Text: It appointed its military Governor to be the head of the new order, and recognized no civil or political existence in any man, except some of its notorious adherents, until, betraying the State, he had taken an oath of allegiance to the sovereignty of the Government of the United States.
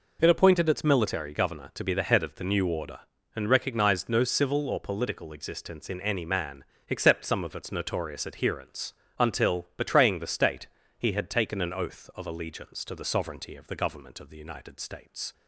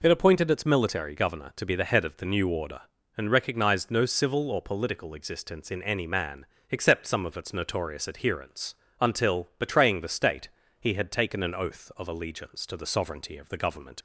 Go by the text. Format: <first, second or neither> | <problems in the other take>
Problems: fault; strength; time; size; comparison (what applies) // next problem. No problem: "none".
first | stops before "of the United States"; at 13.9 s